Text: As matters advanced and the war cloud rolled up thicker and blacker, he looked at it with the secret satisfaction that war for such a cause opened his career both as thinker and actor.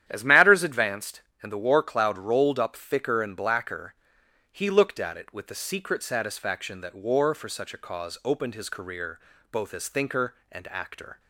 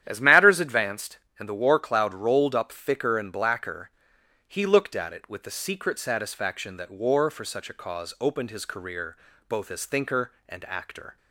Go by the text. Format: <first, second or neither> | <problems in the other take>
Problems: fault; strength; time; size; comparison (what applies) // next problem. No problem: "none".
neither | starts louder than the rest; strong; the same in both // pauses between "career" and "both"; slight; the same in both